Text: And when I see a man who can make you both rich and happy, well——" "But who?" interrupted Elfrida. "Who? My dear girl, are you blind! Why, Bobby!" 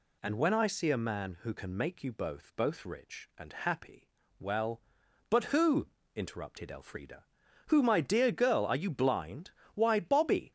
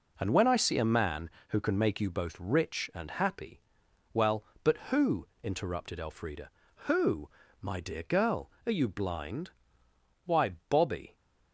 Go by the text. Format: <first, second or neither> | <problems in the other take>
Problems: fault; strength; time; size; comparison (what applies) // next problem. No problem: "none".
second | says "both" twice; at 2.5 s